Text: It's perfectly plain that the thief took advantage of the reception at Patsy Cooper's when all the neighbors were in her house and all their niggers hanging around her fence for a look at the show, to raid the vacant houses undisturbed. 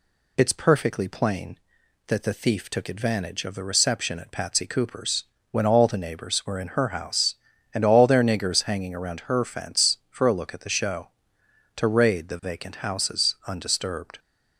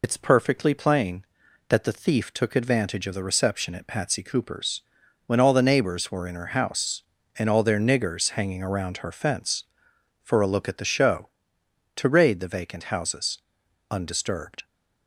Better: first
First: pauses between "Cooper's" and "when"; slight; at 5.2 s; 0.26 s long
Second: loses the start of "It's"; at 0.0 s; 45 ms // pauses between "Cooper's" and "when"; at 4.8 s; 0.44 s long // pauses between "houses" and "undisturbed"; noticeable; at 13.3 s; 0.52 s long

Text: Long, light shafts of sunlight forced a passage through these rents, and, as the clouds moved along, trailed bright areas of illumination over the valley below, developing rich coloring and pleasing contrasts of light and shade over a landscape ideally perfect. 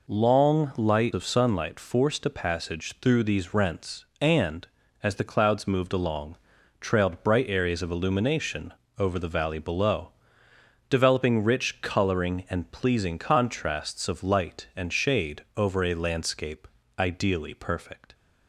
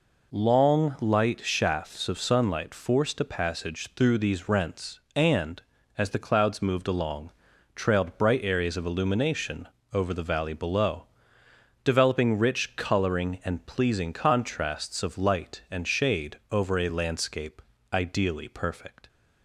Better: second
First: skips "shafts"; at 1.1 s // pauses between "illumination" and "over"; slight; at 8.7 s; 0.26 s long // pauses between "shade" and "over"; slight; at 15.4 s; 0.16 s long // pauses between "landscape" and "ideally"; slight; at 16.6 s; 0.32 s long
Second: pauses between "illumination" and "over"; slight; at 9.6 s; 0.26 s long // pauses between "shade" and "over"; slight; at 16.3 s; 0.16 s long // pauses between "landscape" and "ideally"; slight; at 17.5 s; 0.32 s long

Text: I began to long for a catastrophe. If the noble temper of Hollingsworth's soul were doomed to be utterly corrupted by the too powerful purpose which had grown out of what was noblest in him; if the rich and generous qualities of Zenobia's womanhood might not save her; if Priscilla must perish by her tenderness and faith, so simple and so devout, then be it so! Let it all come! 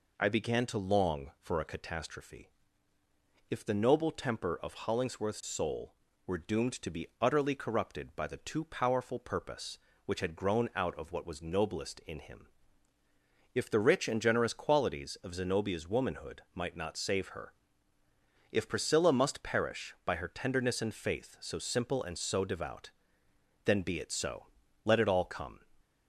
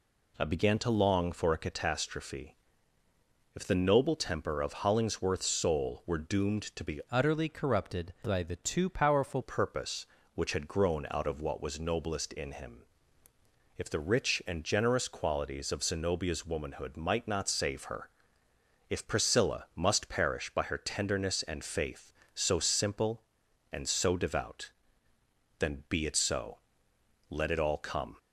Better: first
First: none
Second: changes voice from "utterly" to "powerful"; from 7.0 to 9.4 s; 2.4 s long

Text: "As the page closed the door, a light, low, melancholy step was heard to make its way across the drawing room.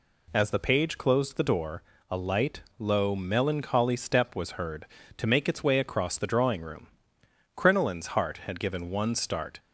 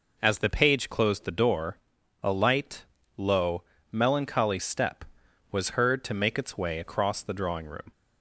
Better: second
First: goes on to say "Crinoline's heart had given one start"; strong; from 7.5 s on; 2.0 s long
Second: none

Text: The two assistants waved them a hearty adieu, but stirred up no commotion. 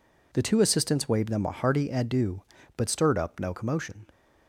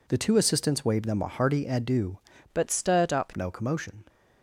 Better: first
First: none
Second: changes voice from "but" to "up"; from 2.5 to 3.3 s; 0.8 s long

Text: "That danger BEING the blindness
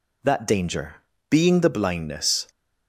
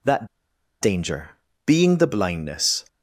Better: first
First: pauses between "danger" and "BEING"; slight; at 0.9 s; 0.34 s long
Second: pauses between "That" and "danger"; noticeable; at 0.2 s; 0.54 s long // pauses between "danger" and "BEING"; slight; at 1.3 s; 0.36 s long

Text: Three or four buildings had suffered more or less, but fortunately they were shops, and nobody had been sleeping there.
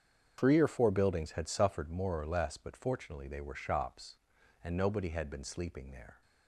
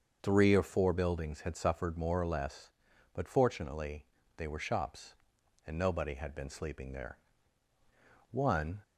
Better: first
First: starts louder than the rest; strong; until 1.3 s; 7.5 dB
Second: starts louder than the rest; until 1.2 s; 6.5 dB // pauses between "fortunately" and "they"; slight; at 4.0 s; 0.32 s long // goes on to say "One"; from 8.3 s on; 0.52 s long

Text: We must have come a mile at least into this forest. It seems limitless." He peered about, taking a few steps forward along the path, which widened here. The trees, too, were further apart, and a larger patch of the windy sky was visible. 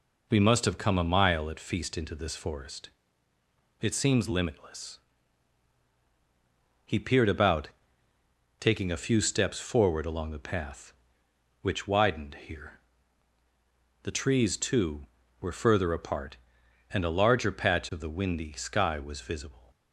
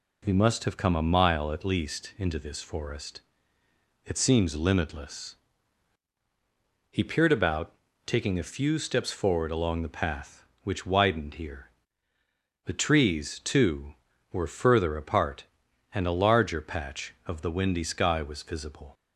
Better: second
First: says "feast" for "least"; at 1.5 s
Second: none

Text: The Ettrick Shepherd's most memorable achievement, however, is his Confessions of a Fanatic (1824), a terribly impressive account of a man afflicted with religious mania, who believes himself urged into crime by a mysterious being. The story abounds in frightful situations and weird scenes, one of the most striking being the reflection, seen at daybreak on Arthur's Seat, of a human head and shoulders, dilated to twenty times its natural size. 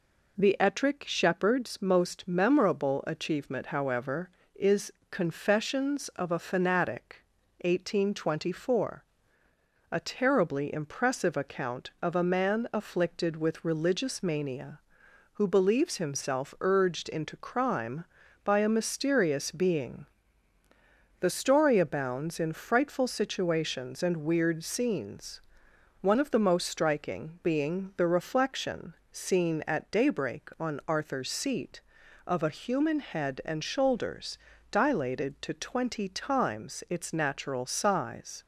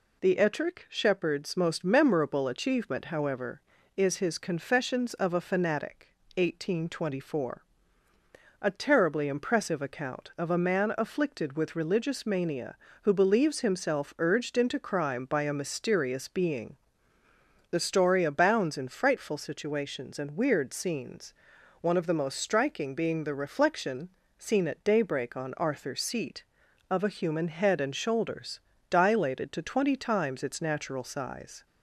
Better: second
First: skips "his"; at 5.0 s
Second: none

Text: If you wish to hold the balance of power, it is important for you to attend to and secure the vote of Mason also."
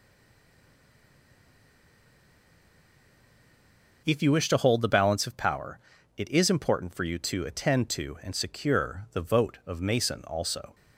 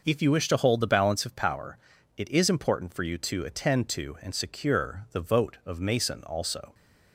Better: second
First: stays silent before the first word; strong; until 4.0 s; 4.0 s long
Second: none

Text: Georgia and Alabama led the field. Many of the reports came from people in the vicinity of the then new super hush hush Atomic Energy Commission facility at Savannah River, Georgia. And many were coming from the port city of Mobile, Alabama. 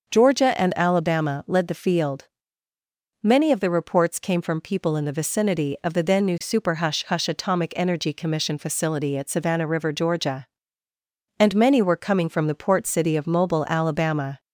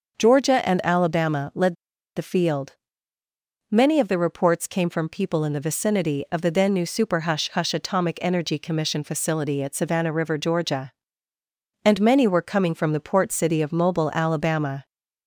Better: first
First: starts louder than the rest; until 1.1 s; 6.5 dB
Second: starts louder than the rest; until 1.2 s; 6.5 dB // pauses between "led" and "the"; at 1.7 s; 0.41 s long

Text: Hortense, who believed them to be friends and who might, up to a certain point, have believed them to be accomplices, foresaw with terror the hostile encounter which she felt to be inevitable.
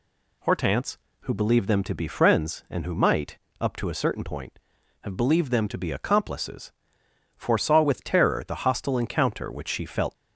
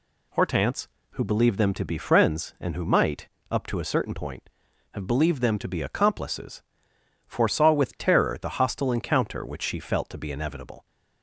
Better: second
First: stops before "to be inevitable"; at 10.1 s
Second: none

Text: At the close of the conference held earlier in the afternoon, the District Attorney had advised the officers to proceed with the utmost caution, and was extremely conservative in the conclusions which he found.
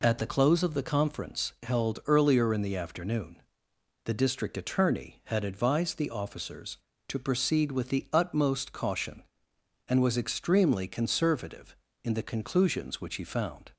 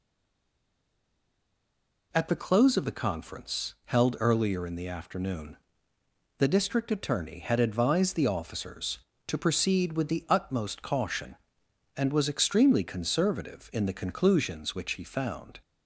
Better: first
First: none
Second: stays silent before the first word; until 2.1 s; 2.1 s long

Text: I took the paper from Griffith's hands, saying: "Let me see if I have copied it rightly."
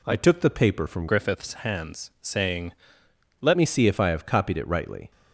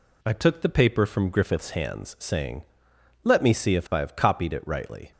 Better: second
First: changes voice from "Griffith's" to "Let"; from 1.0 to 3.5 s; 2.5 s long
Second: none

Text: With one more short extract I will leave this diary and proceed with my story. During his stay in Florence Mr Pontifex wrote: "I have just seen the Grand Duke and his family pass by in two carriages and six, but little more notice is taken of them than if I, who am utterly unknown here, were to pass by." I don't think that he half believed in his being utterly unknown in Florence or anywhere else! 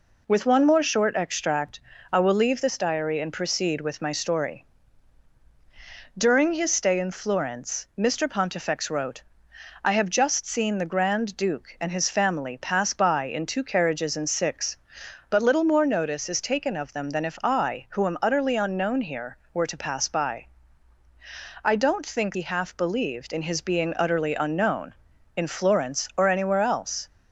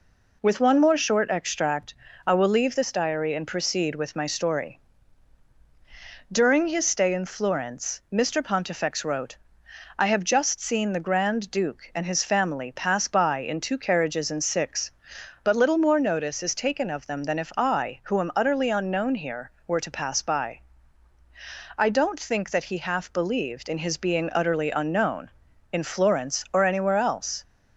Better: second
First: pauses between "extract" and "I"; slight; at 1.8 s; 0.30 s long // skips "that"; at 22.3 s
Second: pauses between "extract" and "I"; slight; at 1.9 s; 0.30 s long

